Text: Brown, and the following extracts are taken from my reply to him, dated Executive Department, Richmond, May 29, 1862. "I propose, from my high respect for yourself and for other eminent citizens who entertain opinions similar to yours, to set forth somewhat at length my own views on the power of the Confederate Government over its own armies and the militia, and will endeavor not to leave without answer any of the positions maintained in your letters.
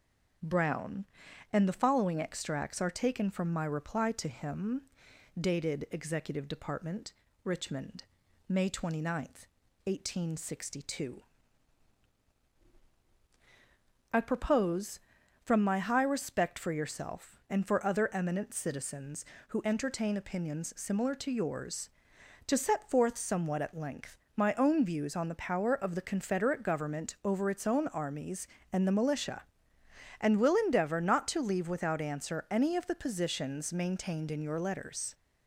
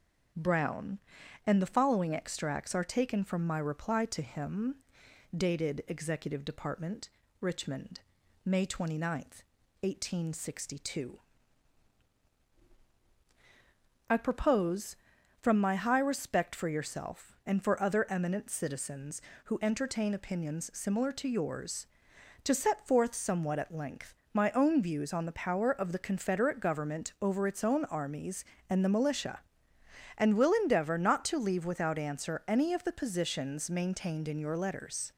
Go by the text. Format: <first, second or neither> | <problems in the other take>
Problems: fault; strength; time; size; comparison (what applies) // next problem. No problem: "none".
neither | starts louder than the rest; the same in both // pauses between "length" and "my"; slight; the same in both